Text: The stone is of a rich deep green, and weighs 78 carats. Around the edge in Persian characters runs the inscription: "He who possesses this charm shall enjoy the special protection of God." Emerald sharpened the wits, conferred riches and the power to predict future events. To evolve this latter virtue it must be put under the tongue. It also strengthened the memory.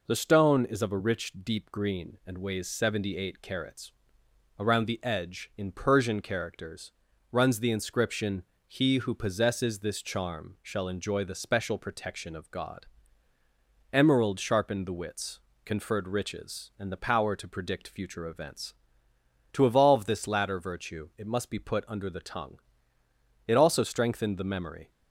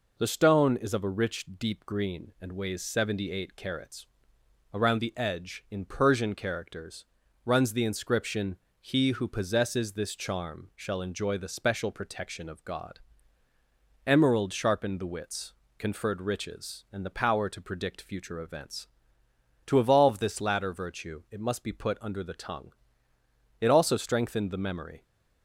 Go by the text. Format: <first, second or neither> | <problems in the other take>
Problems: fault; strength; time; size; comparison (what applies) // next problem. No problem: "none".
neither | pauses between "characters" and "runs"; the same in both